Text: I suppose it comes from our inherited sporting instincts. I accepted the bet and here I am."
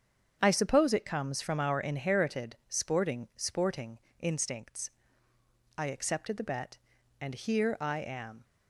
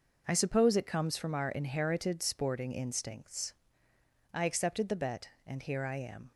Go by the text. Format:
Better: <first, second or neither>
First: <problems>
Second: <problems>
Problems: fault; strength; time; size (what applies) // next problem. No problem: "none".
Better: second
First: starts louder than the rest; strong; until 1.4 s; 8 dB // says "sporting" twice; at 3.3 s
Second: none